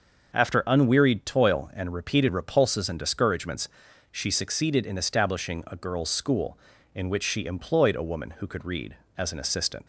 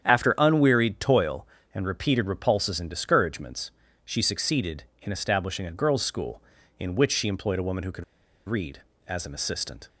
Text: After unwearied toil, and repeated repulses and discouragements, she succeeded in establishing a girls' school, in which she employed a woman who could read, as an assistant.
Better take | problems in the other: first | starts louder than the rest; strong; until 1.0 s; 8.5 dB; also in the first // pauses between "could" and "read"; at 8.0 s; 0.43 s long

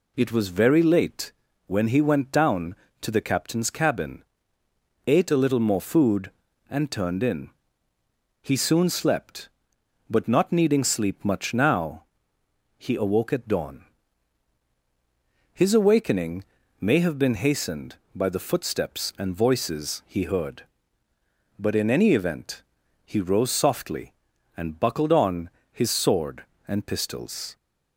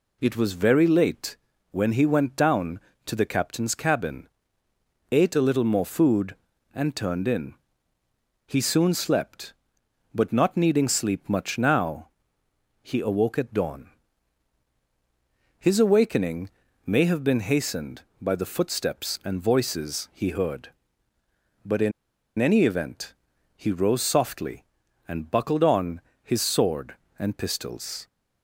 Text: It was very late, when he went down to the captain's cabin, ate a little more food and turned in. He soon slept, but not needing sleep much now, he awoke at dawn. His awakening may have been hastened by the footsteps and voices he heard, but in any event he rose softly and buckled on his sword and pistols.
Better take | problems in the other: first | pauses between "awakening" and "may"; at 16.4 s; 0.38 s long; also in the first // pauses between "in" and "any"; noticeable; at 21.9 s; 0.47 s long // pauses between "event" and "he"; at 23.1 s; 0.40 s long; also in the first // pauses between "on" and "his"; slight; at 26.0 s; 0.22 s long; slight in the first

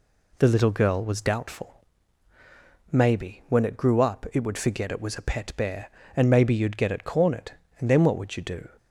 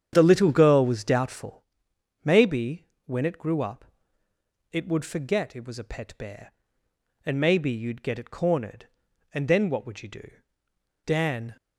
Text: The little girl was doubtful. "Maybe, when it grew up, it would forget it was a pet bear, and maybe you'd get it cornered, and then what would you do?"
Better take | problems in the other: first | starts louder than the rest; strong; until 1.1 s; 9 dB // goes on to say "Dan"; from 11.0 s on; 0.52 s long

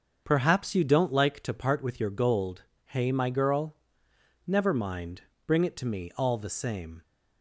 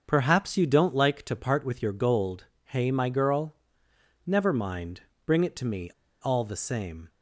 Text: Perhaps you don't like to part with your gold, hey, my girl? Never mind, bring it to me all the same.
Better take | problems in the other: first | starts louder than the rest; until 1.0 s; 6.5 dB; also in the first // pauses between "me" and "all"; slight; at 5.9 s; 0.31 s long

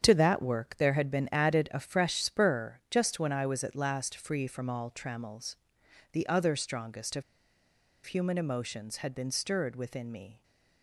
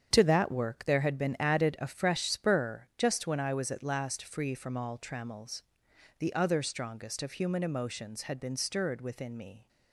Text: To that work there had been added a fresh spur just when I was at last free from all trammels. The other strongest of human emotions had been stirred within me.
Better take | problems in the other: second | starts louder than the rest; strong; until 1.0 s; 8 dB; strong in the second // pauses between "of" and "human"; noticeable; at 7.2 s; 0.83 s long

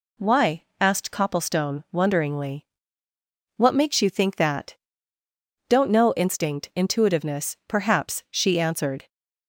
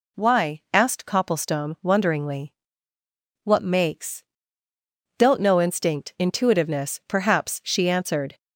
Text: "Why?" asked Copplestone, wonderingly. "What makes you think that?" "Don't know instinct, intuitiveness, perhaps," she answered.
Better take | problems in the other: first | skips "you think that"; at 4.7 s

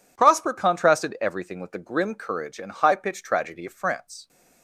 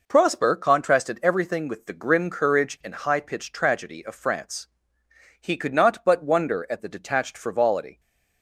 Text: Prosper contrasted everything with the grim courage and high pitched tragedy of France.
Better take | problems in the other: first | goes on to say "He could not but wonder at the detached frivolity"; strong; from 5.3 s on; 2.6 s long

